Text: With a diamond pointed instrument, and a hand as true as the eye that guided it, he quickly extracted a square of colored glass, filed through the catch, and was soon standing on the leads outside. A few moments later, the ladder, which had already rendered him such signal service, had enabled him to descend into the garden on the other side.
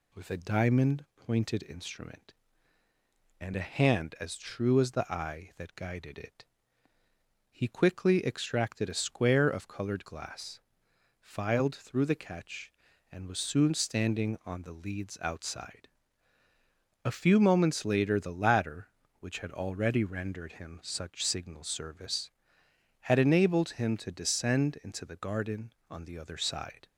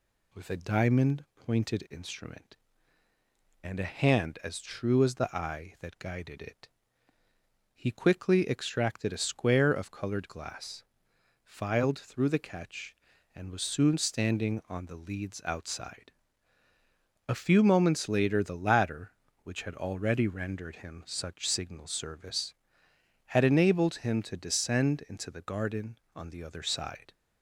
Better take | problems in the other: neither | none

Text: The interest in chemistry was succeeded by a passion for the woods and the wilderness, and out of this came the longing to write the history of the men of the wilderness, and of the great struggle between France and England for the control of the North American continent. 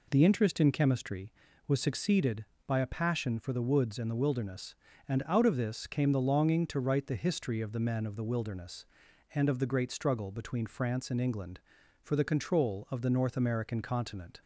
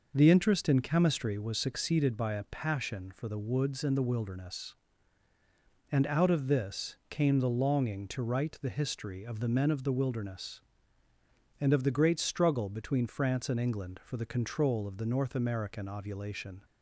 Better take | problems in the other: first | says "ovulation" for "continent"; at 15.8 s

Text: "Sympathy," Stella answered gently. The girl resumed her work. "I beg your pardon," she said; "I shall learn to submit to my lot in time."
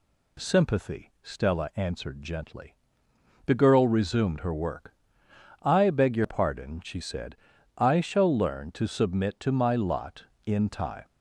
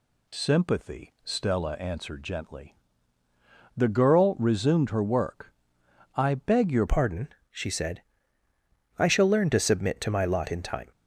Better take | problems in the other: first | changes voice at "pardon"; from 6.8 s on; 4.1 s long

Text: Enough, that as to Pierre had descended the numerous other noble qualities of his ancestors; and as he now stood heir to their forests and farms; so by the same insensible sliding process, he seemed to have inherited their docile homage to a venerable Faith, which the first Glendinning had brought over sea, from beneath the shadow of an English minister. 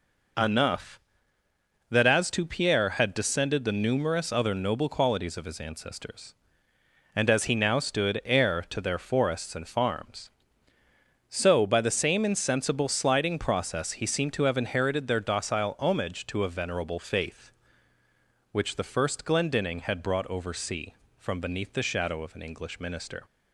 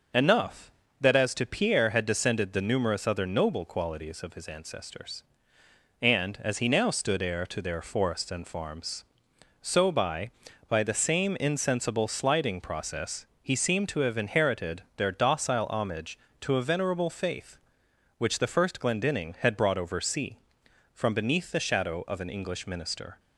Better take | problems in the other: first | starts louder than the rest; noticeable; until 1.4 s; 6 dB // says "by" twice; at 10.6 s

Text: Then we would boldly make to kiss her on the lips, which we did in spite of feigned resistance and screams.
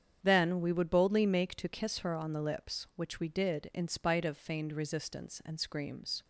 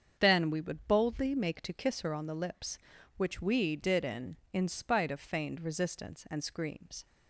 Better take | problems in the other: first | starts louder than the rest; strong; until 1.2 s; 7 dB; strong in the first // says "in" twice; at 4.5 s

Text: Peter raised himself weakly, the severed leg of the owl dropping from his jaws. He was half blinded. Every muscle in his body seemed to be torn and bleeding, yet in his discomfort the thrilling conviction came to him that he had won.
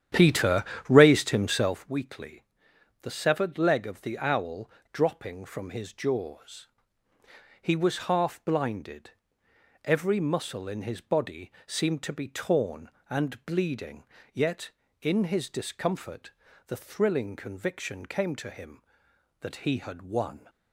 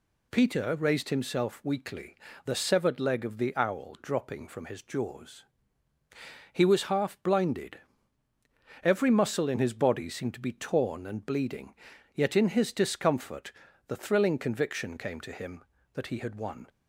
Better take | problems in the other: second | starts louder than the rest; strong; until 1.9 s; 10 dB // pauses between "Peter" and "raised"; slight; at 0.6 s; 0.24 s long // pauses between "owl" and "dropping"; slight; at 4.6 s; 0.22 s long // pauses between "discomfort" and "the"; at 16.2 s; 0.38 s long; slight in the second

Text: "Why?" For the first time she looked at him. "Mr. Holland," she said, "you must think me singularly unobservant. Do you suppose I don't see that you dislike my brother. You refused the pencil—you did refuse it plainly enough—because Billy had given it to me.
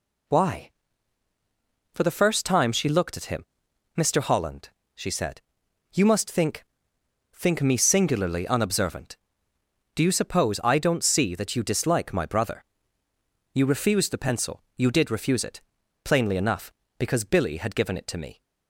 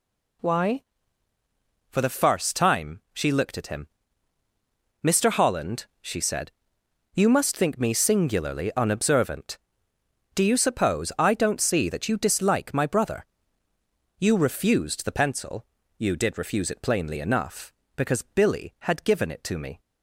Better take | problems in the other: second | says "think" twice; at 7.3 s // pauses between "it" and "plainly"; at 15.6 s; 0.44 s long

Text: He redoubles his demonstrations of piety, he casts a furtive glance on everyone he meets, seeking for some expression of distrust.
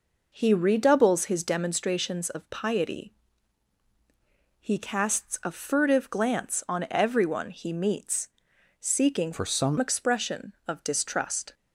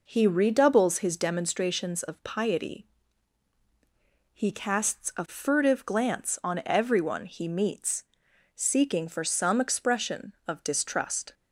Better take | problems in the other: second | changes voice from "for" to "some"; from 9.3 to 9.7 s; 0.4 s long

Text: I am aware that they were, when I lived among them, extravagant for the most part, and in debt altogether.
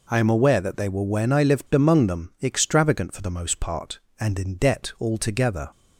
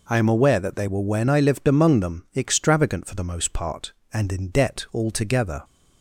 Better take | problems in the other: neither | none

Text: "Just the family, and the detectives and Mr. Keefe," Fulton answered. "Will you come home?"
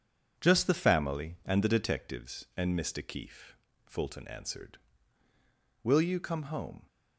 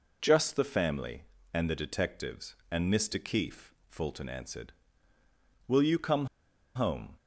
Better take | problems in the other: first | pauses between "come" and "home"; noticeable; at 6.2 s; 0.49 s long

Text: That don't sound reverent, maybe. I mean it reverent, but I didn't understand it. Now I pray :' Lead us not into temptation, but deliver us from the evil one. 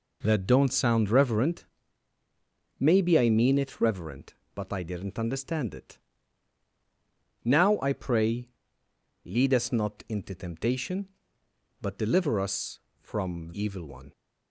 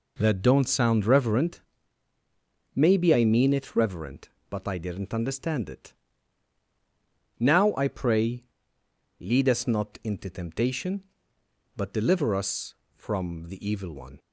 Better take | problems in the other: second | skips "the"; at 13.5 s

